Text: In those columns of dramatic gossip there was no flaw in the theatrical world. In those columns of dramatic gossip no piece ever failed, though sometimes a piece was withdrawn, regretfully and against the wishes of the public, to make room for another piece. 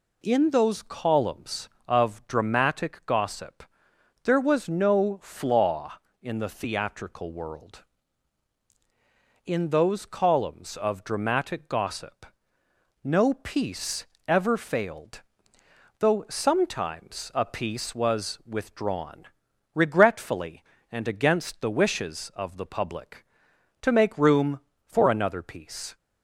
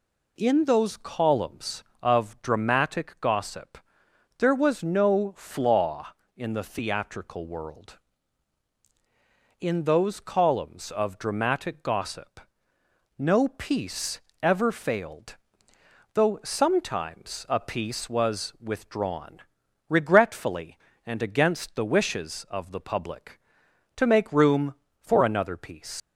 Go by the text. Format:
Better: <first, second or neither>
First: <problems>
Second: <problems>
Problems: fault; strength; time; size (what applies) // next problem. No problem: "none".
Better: first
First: pauses between "gossip" and "there"; noticeable; at 3.6 s; 0.58 s long // pauses between "gossip" and "no"; noticeable; at 12.2 s; 0.78 s long // pauses between "piece" and "ever"; slight; at 14.0 s; 0.22 s long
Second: pauses between "gossip" and "there"; noticeable; at 3.7 s; 0.58 s long // pauses between "gossip" and "no"; noticeable; at 12.3 s; 0.78 s long // pauses between "piece" and "ever"; slight; at 14.2 s; 0.22 s long // leaves "piece" unfinished; at 26.0 s; 105 ms